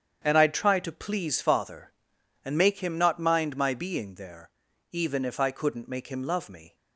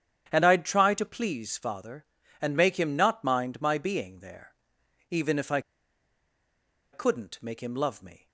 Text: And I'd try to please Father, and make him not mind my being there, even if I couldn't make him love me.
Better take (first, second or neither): first